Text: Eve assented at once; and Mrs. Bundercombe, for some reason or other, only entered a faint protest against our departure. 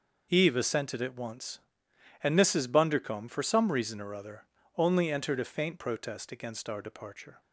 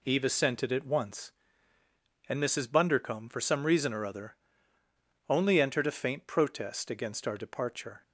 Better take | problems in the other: neither | none

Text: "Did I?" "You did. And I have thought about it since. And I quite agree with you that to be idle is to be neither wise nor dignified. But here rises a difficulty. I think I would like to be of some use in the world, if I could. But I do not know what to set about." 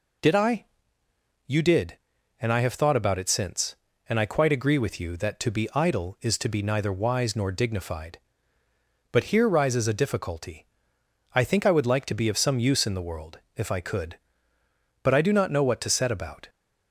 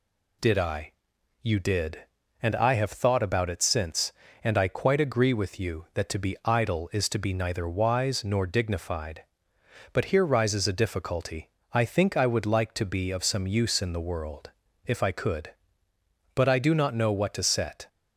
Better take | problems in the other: first | stops before "about"; at 17.8 s

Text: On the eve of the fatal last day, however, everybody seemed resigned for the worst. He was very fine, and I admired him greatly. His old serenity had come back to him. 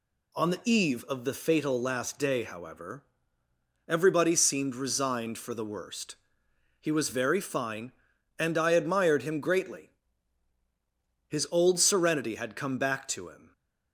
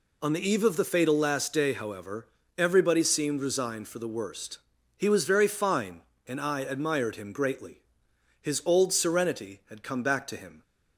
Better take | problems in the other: neither | none

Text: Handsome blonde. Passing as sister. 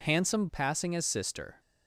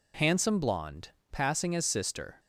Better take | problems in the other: second | skips "blonde"; at 0.4 s

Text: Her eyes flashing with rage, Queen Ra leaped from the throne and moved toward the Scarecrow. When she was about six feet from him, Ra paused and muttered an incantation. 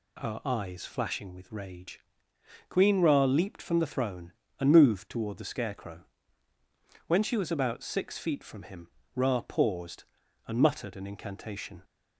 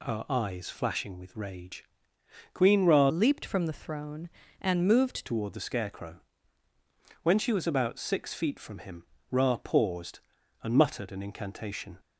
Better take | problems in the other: first | changes voice from "leaped" to "moved"; from 3.0 to 5.2 s; 2.2 s long

